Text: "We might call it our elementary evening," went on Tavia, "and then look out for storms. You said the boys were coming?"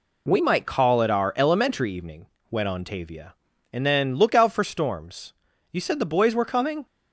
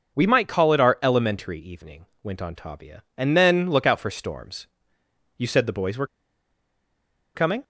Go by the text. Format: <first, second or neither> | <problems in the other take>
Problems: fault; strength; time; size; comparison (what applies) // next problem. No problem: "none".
first | starts louder than the rest; until 1.2 s; 6 dB // pauses between "were" and "coming"; strong; at 6.0 s; 1.2 s long